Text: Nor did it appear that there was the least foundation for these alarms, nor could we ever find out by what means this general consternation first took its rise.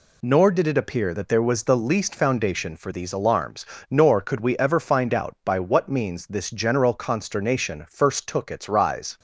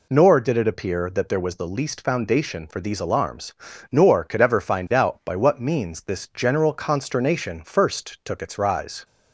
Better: first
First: none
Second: skips "we"; at 4.3 s

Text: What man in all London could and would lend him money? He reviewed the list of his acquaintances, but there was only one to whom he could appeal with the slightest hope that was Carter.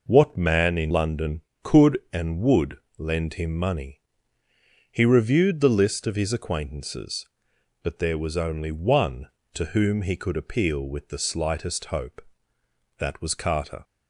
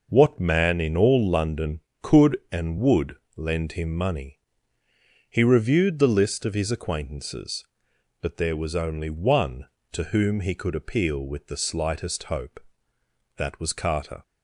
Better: second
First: skips "all"; at 0.9 s // pauses between "would" and "lend"; slight; at 2.7 s; 0.20 s long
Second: pauses between "would" and "lend"; slight; at 3.1 s; 0.20 s long

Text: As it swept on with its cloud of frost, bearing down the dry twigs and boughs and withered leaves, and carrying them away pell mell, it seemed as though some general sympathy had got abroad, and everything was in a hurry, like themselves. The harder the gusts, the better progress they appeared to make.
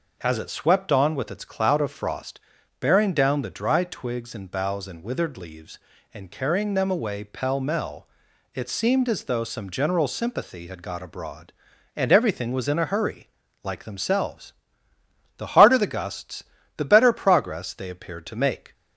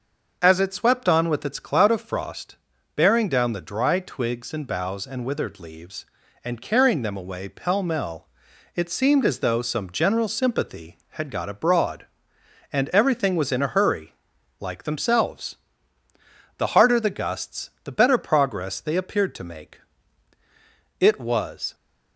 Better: first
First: none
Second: starts louder than the rest; until 1.4 s; 6 dB // goes on to say "It was"; noticeable; from 21.0 s on; 0.74 s long

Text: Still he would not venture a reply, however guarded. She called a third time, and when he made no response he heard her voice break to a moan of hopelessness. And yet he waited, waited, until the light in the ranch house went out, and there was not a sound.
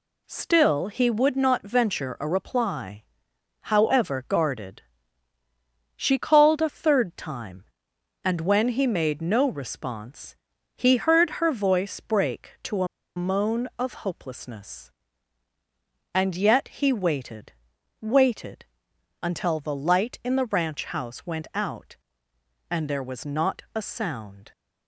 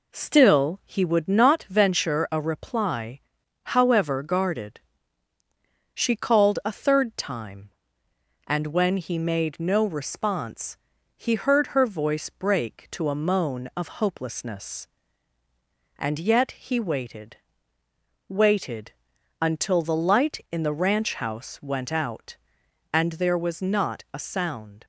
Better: second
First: pauses between "response" and "he"; at 10.3 s; 0.38 s long // pauses between "a" and "moan"; slight; at 12.8 s; 0.30 s long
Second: pauses between "response" and "he"; at 10.7 s; 0.44 s long

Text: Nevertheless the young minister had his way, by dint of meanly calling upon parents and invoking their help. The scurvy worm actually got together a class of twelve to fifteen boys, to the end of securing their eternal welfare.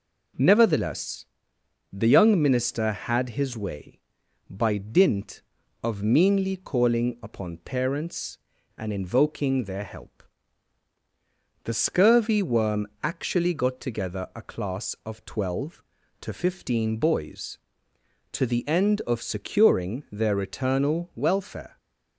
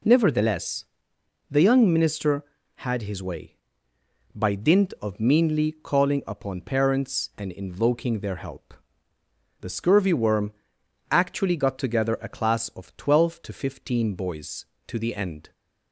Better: first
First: pauses between "Nevertheless" and "the"; noticeable; at 1.2 s; 0.68 s long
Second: pauses between "Nevertheless" and "the"; noticeable; at 0.8 s; 0.66 s long // pauses between "worm" and "actually"; noticeable; at 10.5 s; 0.60 s long // stops before "of securing their eternal welfare"; at 15.5 s

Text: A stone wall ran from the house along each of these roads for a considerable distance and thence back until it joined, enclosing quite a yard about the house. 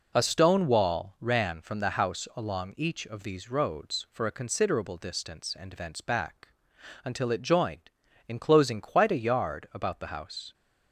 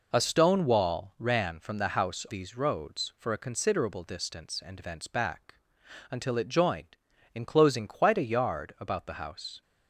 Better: first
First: pauses between "back" and "until"; noticeable; at 6.4 s; 0.56 s long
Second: skips "along each of"; at 2.2 s // pauses between "back" and "until"; noticeable; at 5.5 s; 0.56 s long

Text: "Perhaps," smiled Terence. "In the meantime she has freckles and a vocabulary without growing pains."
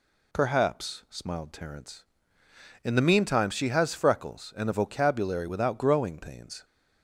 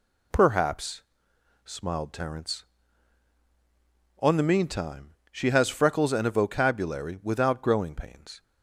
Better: first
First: none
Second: says "On" for "In"; at 4.1 s // pauses between "meantime" and "she"; slight; at 5.1 s; 0.16 s long

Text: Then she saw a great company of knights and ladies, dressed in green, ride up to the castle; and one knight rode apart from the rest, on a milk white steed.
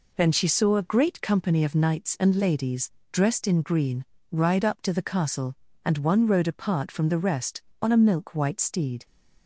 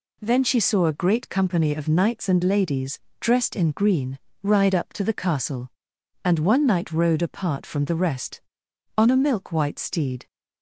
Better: second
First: skips "knight"; at 6.2 s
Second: none

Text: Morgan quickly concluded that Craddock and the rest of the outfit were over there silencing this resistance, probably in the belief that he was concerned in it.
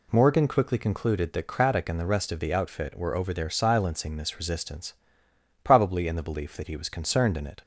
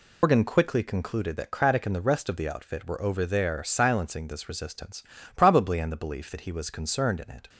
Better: first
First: none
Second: loses the start of "Morgan"; at 0.2 s; 125 ms

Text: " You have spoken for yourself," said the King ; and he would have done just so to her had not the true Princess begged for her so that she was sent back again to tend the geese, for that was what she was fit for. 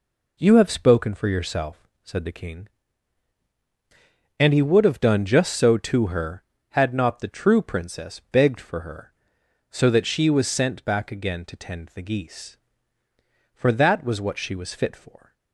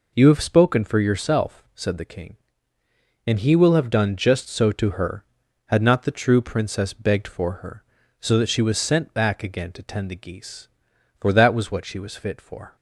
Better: first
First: none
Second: says "will" for "would"; at 3.5 s

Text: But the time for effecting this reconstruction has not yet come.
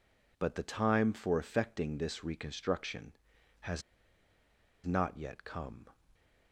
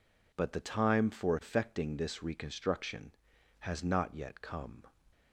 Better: second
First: pauses between "has" and "not"; at 3.8 s; 1.0 s long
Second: none

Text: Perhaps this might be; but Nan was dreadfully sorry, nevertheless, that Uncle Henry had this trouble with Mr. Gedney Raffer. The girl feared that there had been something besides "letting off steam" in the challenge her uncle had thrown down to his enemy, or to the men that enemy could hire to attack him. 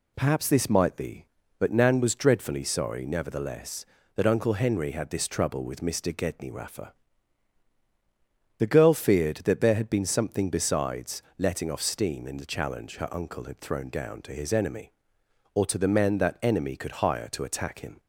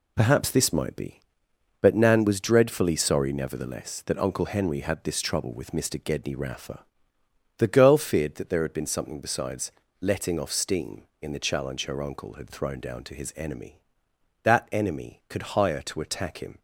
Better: first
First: pauses between "besides" and "letting"; slight; at 11.1 s; 0.16 s long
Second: pauses between "besides" and "letting"; slight; at 9.7 s; 0.30 s long // skips "or to the men"; at 14.1 s

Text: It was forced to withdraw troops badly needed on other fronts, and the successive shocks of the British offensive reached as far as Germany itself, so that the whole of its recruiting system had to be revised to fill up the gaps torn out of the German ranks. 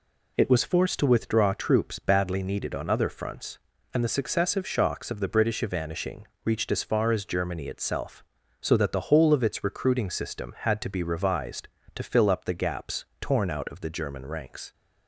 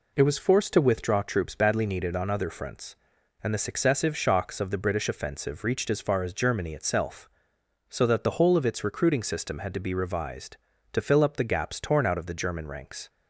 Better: second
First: says "evanishing" for "offensive"; at 5.6 s // pauses between "gaps" and "torn"; slight; at 13.0 s; 0.16 s long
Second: none

